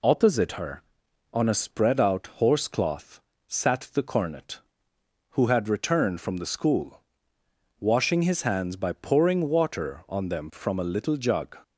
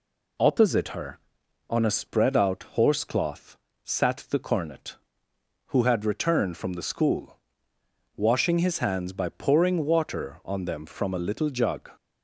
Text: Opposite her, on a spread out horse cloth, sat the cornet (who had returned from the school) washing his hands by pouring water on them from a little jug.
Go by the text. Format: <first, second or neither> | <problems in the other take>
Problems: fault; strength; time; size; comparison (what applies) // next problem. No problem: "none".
neither | none